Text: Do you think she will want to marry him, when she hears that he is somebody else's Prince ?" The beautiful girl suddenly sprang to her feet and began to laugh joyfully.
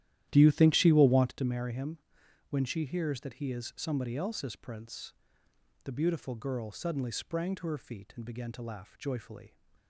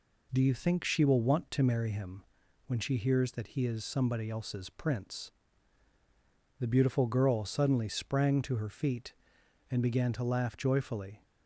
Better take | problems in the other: second | starts louder than the rest; strong; until 1.4 s; 12.5 dB

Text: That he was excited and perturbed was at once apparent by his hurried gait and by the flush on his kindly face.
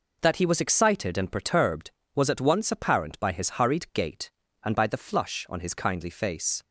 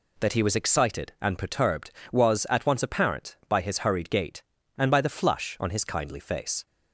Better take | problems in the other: neither | none

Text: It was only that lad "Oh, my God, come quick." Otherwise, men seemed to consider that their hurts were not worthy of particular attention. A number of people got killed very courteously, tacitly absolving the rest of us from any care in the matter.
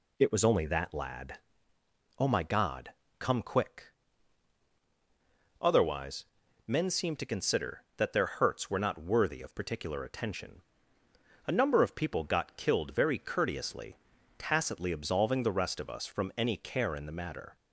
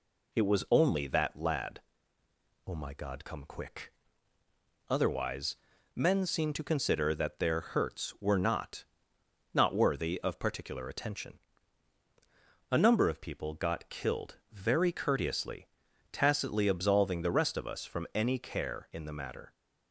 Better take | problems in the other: first | pauses between "lad" and "Oh"; noticeable; at 1.8 s; 0.84 s long; noticeable in the first // says "not" twice; at 9.5 s // pauses between "killed" and "very"; slight; at 14.3 s; 0.16 s long

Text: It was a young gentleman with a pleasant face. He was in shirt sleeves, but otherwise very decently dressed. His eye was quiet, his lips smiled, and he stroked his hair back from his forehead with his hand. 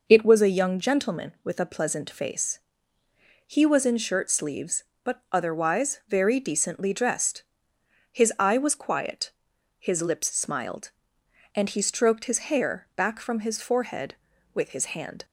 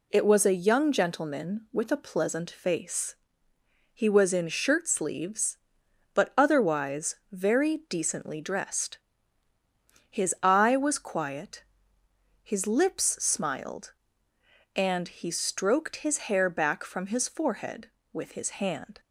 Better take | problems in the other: neither | none

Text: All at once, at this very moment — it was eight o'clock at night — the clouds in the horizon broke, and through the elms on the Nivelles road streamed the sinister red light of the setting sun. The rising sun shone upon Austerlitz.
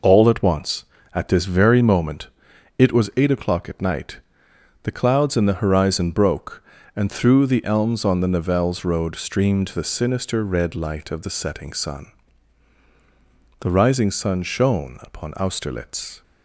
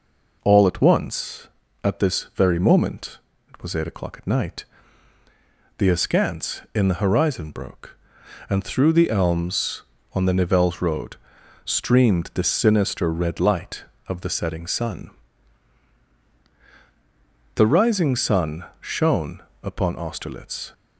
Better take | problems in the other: first | says "askance" for "clouds"; at 5.8 s // pauses between "road" and "streamed"; noticeable; at 11.1 s; 0.48 s long // pauses between "sun" and "shone"; slight; at 18.6 s; 0.16 s long // pauses between "shone" and "upon"; slight; at 19.4 s; 0.20 s long

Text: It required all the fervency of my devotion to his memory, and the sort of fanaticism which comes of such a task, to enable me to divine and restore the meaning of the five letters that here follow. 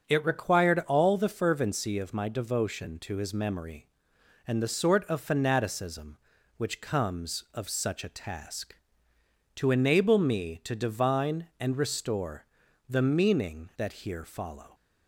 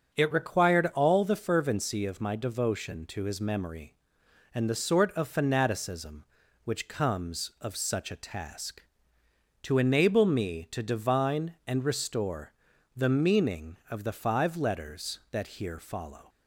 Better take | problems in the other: second | starts louder than the rest; until 1.1 s; 7 dB; also in the second // pauses between "restore" and "the"; at 12.4 s; 0.42 s long; also in the second // skips "of the five letters"; at 13.7 s

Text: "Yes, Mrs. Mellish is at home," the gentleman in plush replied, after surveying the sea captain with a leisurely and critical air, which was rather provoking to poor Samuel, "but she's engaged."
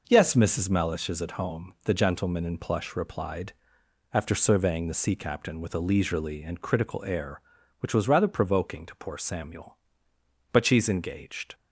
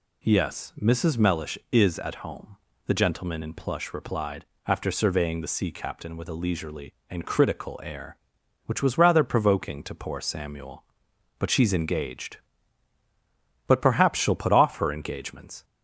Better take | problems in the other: first | goes on to say "But perhaps she'll put off her engagements"; strong; from 13.6 s on; 1.9 s long

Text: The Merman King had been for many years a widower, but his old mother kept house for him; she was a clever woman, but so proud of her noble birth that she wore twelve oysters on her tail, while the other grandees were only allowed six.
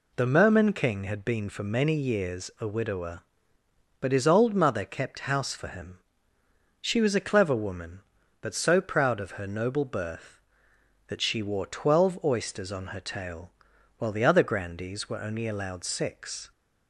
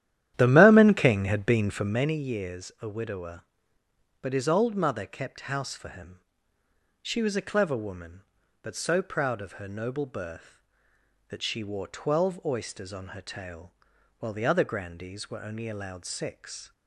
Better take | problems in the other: first | starts louder than the rest; strong; until 2.1 s; 11.5 dB

